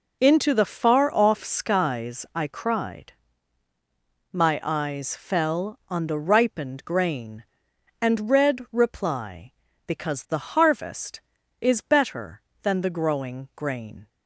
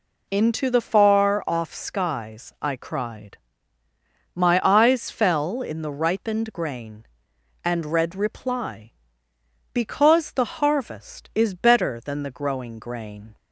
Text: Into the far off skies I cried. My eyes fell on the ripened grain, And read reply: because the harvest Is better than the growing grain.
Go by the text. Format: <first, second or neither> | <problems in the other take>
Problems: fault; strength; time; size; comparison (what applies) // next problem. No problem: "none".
first | says "in" for "on"; at 5.6 s